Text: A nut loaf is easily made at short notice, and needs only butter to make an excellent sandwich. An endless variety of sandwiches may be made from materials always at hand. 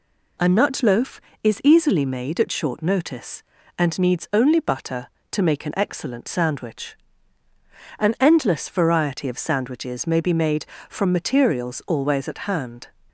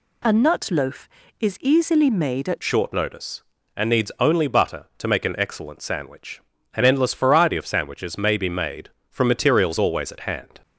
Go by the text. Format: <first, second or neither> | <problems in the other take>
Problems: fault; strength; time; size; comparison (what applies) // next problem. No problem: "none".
first | changes voice at "short"; from 2.6 s on; 8.0 s long